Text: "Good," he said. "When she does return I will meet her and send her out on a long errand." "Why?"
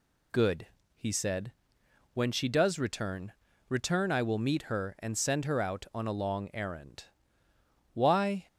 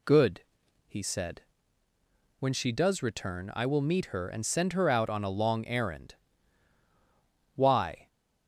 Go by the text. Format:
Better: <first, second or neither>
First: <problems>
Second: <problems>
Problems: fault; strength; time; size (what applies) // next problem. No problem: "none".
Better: second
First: says "return" twice; at 3.6 s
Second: none